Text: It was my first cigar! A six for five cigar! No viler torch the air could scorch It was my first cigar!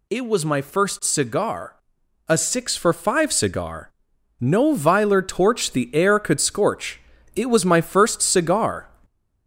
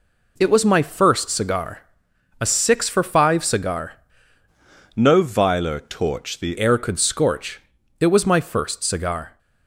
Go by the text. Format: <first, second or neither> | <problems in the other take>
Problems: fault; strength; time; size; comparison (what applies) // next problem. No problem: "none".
first | changes voice from "No" to "the"; from 4.9 to 6.5 s; 1.6 s long // pauses between "scorch" and "It"; at 7.5 s; 0.40 s long; slight in the first